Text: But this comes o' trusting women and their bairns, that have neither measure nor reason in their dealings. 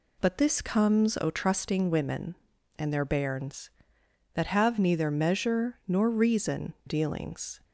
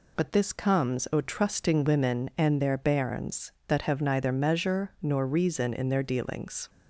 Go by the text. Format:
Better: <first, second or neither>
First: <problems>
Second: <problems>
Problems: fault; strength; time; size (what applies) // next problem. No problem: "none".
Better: second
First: skips "in their"; at 6.7 s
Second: none